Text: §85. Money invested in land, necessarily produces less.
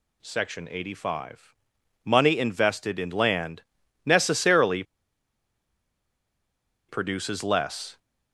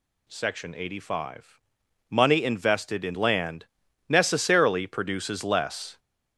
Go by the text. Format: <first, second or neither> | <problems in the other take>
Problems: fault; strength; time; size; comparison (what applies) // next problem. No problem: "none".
second | pauses between "necessarily" and "produces"; strong; at 4.8 s; 2.0 s long